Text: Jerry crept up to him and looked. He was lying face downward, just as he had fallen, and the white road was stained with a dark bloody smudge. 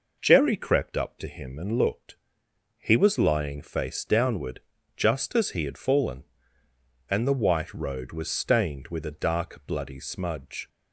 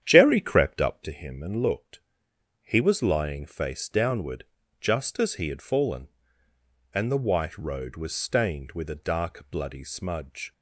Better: first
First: none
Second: starts louder than the rest; strong; until 1.1 s; 9.5 dB

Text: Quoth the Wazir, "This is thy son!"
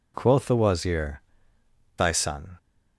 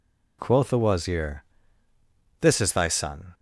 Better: second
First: skips "This is"; at 1.5 s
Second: none

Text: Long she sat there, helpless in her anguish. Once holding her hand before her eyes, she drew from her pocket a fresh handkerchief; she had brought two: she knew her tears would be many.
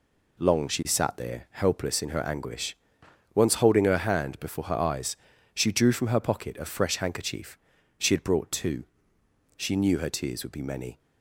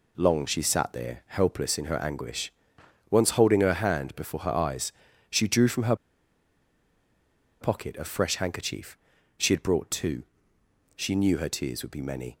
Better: first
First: none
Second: pauses between "her" and "pocket"; strong; at 5.9 s; 1.6 s long

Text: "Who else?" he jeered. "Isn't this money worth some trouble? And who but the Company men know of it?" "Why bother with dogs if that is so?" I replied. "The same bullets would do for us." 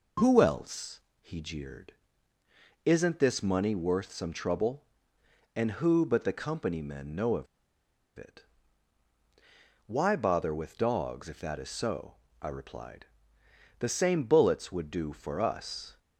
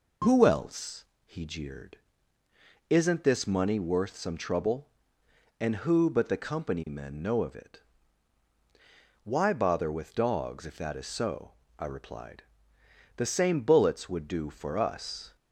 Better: second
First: pauses between "of" and "it"; noticeable; at 7.4 s; 0.71 s long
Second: none

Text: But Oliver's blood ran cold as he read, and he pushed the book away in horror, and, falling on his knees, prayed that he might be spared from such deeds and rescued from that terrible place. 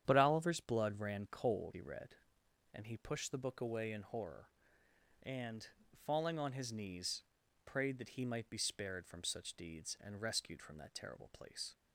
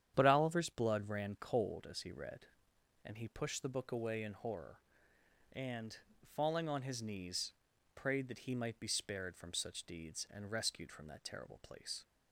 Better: second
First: starts louder than the rest; strong; until 1.0 s; 9.5 dB // skips "as"; at 1.7 s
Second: starts louder than the rest; strong; until 1.1 s; 9.5 dB

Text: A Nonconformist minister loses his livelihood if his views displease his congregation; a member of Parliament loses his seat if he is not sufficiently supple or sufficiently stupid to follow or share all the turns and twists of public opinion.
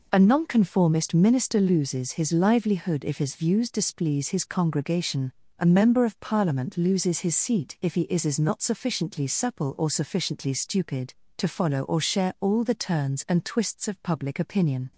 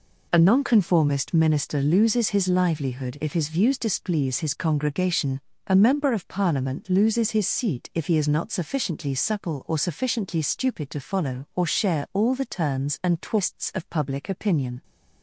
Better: second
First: says "is" twice; at 8.2 s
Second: none

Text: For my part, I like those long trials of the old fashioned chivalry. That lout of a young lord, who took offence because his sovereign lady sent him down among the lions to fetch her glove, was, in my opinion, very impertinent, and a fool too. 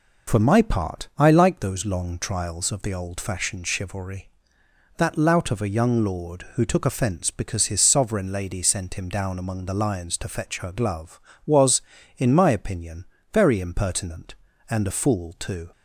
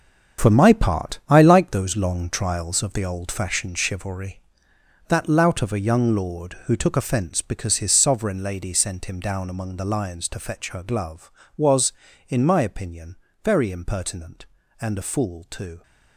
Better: first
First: none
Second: gets quieter; strong; throughout; 10.5 dB

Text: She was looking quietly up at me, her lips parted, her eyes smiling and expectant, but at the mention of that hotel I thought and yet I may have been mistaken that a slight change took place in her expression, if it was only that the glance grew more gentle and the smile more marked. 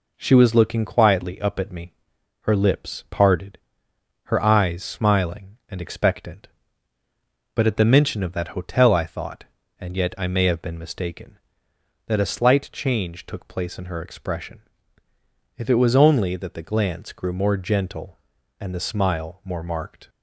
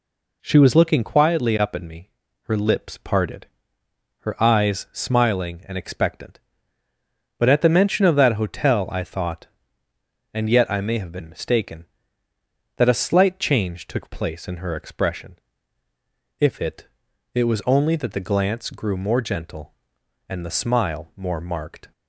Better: first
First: none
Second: says "it" twice; at 17.3 s

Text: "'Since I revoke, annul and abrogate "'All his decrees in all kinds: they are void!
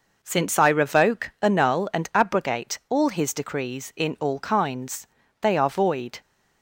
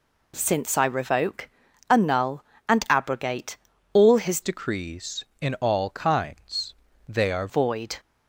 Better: first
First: none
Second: pauses between "abrogate" and "All"; at 3.5 s; 0.38 s long // changes voice from "decrees" to "are"; from 4.4 to 7.4 s; 3.0 s long

